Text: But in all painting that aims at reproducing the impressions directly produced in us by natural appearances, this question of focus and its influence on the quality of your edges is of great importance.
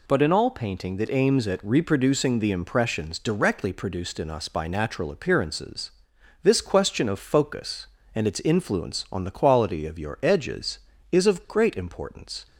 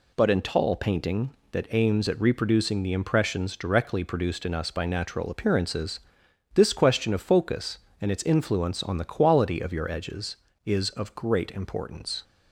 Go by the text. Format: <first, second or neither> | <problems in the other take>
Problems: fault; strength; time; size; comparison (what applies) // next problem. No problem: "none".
first | says "tall" for "all"; at 0.4 s